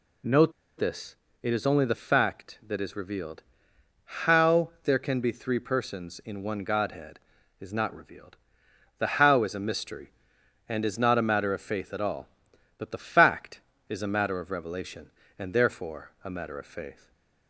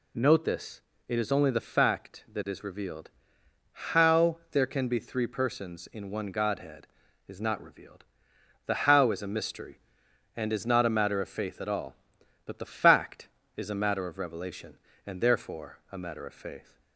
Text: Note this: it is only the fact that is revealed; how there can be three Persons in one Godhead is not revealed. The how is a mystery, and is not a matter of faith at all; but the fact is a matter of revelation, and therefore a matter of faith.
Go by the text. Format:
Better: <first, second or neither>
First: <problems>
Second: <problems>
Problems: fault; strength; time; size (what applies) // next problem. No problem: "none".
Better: second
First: pauses between "Note" and "this"; slight; at 0.5 s; 0.28 s long // stays silent after the last word; slight; from 16.9 s on; 0.5 s long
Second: none